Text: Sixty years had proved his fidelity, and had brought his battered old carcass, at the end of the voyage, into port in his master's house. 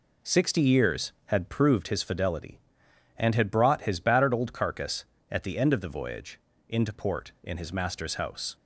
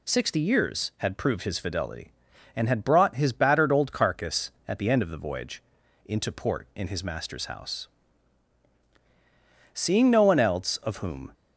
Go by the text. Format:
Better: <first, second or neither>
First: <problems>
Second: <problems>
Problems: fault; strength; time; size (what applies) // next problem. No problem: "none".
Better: first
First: none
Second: goes on to say "Seeing no one else of whom"; from 9.7 s on; 1.5 s long